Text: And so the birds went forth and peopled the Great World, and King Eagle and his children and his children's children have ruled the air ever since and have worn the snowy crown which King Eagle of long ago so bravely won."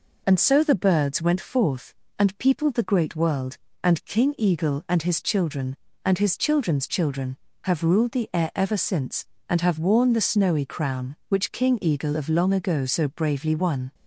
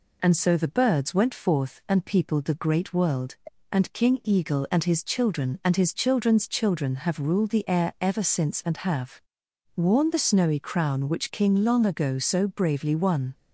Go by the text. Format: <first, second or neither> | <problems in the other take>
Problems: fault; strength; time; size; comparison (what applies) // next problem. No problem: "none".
first | pauses between "have" and "worn"; noticeable; at 9.2 s; 0.54 s long // skips "Eagle of"; at 11.6 s